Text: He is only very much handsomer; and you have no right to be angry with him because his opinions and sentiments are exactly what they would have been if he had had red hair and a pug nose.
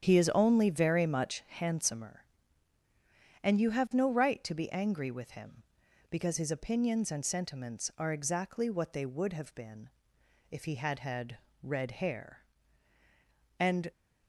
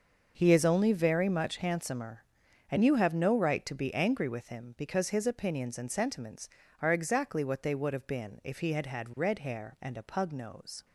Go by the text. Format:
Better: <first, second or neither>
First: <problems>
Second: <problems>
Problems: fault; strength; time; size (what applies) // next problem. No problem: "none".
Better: second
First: starts louder than the rest; strong; until 1.1 s; 9 dB // pauses between "been" and "if"; noticeable; at 9.8 s; 0.60 s long // pauses between "had" and "red"; slight; at 11.3 s; 0.22 s long // stops before "a pug nose"; at 13.9 s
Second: starts louder than the rest; until 1.3 s; 6 dB